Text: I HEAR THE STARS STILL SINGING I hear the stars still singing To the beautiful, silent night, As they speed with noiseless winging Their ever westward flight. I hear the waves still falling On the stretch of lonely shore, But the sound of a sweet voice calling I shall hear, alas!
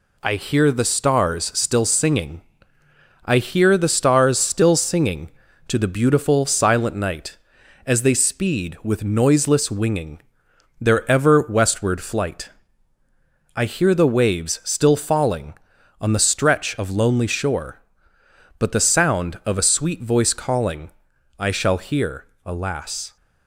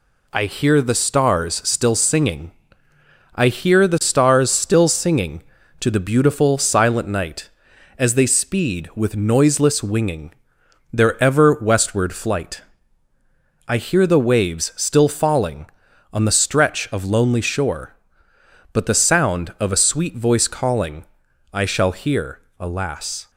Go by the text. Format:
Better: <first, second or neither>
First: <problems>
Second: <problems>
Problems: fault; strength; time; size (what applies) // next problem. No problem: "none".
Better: neither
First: pauses between "SINGING" and "I"; noticeable; at 2.4 s; 0.82 s long // pauses between "winging" and "Their"; noticeable; at 10.1 s; 0.60 s long // pauses between "calling" and "I"; noticeable; at 20.9 s; 0.46 s long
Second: pauses between "SINGING" and "I"; noticeable; at 2.5 s; 0.82 s long // pauses between "winging" and "Their"; noticeable; at 10.3 s; 0.60 s long // pauses between "calling" and "I"; noticeable; at 21.0 s; 0.46 s long